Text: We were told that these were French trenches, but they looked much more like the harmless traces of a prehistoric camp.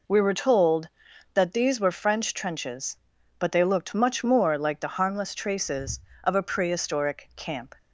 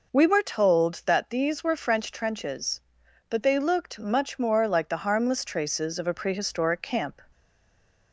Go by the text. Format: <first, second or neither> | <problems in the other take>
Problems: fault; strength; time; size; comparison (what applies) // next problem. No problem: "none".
first | stays silent after the last word; slight; from 7.3 s on; 0.8 s long